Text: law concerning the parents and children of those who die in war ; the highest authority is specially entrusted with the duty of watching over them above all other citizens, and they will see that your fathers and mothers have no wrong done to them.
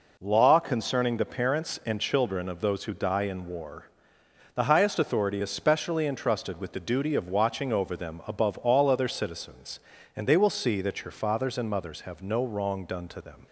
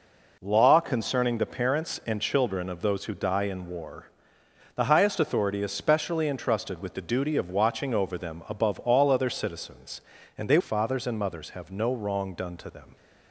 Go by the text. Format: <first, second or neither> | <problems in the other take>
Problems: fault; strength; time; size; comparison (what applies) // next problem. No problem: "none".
first | skips "will see that your"; at 10.5 s